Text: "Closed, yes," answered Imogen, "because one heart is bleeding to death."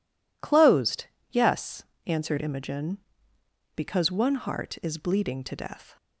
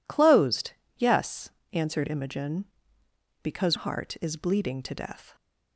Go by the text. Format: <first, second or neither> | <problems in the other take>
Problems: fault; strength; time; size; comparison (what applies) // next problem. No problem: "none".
first | skips "one"; at 3.7 s